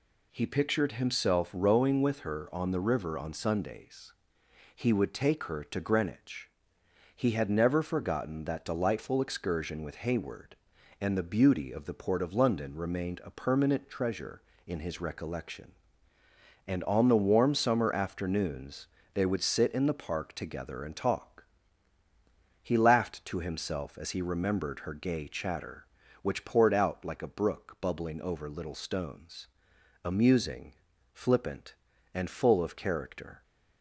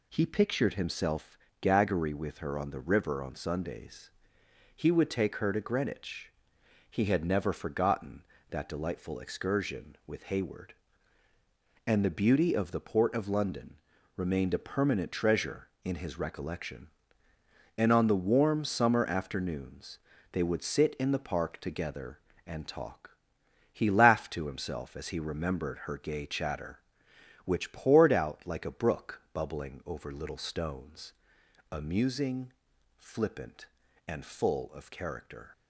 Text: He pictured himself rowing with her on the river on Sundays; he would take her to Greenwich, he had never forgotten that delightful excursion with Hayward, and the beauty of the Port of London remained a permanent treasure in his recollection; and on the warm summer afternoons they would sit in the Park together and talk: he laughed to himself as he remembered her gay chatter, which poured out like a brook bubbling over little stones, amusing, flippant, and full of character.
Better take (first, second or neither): first